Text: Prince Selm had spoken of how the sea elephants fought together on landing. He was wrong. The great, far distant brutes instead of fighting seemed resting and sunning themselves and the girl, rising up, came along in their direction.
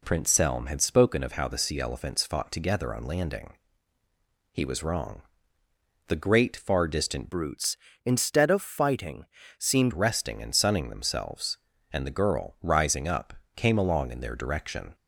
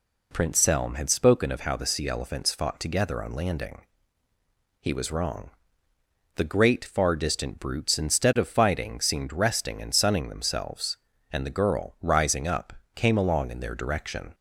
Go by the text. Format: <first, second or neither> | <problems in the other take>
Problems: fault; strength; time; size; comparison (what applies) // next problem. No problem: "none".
second | changes voice from "brutes" to "seemed"; from 7.3 to 9.9 s; 2.6 s long // pauses between "fighting" and "seemed"; slight; at 9.2 s; 0.32 s long